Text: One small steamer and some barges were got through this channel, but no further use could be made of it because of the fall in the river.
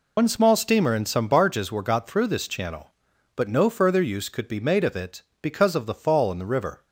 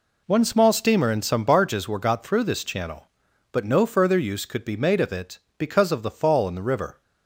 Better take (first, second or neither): second